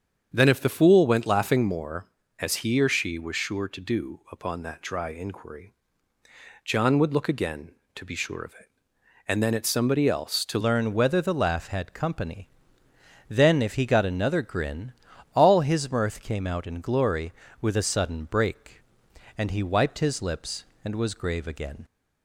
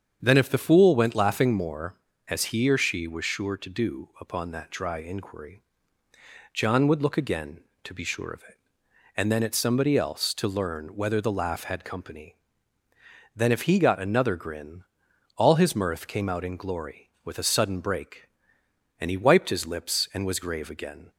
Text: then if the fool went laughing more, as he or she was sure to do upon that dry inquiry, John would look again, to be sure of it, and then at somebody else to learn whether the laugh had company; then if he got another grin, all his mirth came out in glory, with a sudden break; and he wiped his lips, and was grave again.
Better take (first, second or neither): second